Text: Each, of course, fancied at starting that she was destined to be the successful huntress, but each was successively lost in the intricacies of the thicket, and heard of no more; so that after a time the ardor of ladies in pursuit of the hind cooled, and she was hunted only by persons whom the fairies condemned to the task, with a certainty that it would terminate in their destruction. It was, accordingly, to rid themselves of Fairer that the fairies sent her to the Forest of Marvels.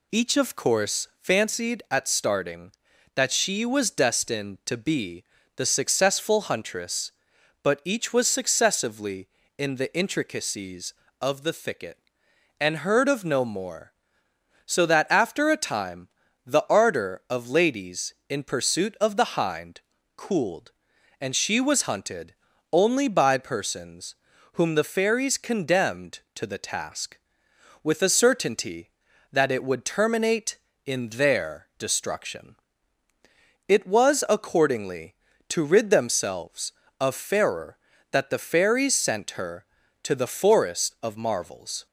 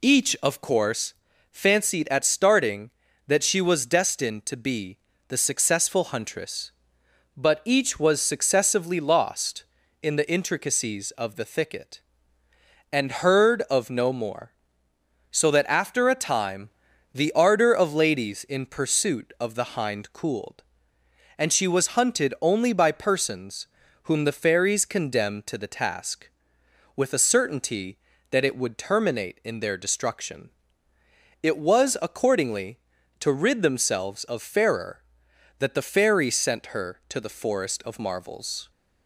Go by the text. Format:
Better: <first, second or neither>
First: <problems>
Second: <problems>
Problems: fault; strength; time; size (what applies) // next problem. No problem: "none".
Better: second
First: pauses between "be" and "the"; slight; at 5.2 s; 0.32 s long // skips "lost"; at 9.4 s // pauses between "time" and "the"; at 16.0 s; 0.38 s long // pauses between "hind" and "cooled"; slight; at 19.8 s; 0.34 s long // pauses between "hunted" and "only"; at 22.3 s; 0.38 s long // pauses between "persons" and "whom"; at 24.1 s; 0.38 s long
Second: pauses between "be" and "the"; slight; at 4.9 s; 0.30 s long // pauses between "time" and "the"; at 16.7 s; 0.42 s long // pauses between "persons" and "whom"; at 23.6 s; 0.38 s long